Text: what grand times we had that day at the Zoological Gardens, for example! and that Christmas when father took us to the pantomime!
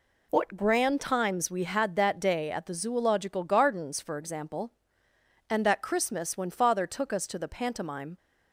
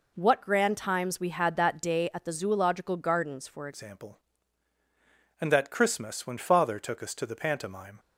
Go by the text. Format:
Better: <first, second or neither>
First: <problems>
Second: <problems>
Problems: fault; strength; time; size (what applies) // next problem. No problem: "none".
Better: first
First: none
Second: changes voice at "example"; from 3.7 s on; 4.2 s long